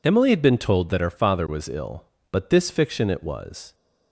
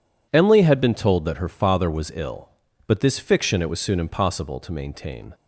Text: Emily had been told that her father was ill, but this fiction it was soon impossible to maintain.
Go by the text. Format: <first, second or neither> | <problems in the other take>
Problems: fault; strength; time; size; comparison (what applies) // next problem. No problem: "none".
second | stops before "soon impossible to maintain"; at 3.7 s